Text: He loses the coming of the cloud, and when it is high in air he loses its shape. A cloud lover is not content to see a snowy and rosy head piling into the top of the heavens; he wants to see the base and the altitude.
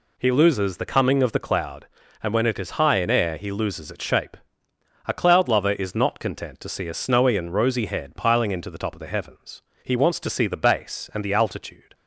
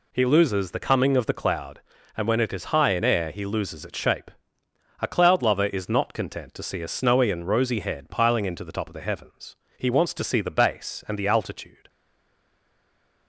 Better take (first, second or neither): first